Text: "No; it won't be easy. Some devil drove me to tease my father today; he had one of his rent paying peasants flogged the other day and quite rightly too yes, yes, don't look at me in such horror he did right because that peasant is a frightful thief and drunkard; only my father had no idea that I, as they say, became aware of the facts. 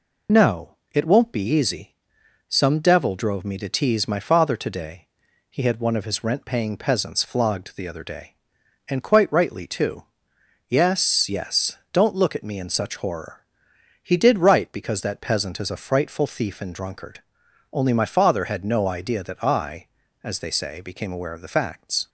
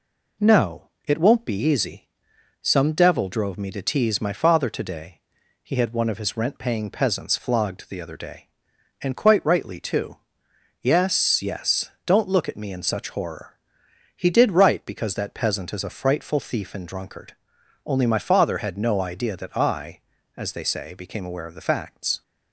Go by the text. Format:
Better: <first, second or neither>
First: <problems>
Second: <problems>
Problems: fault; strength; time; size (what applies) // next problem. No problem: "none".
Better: second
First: loses the start of "No"; at 0.2 s; 30 ms // pauses between "too" and "yes"; noticeable; at 10.0 s; 0.64 s long // pauses between "horror" and "he"; noticeable; at 13.4 s; 0.58 s long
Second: pauses between "too" and "yes"; noticeable; at 10.1 s; 0.64 s long // pauses between "horror" and "he"; noticeable; at 13.5 s; 0.58 s long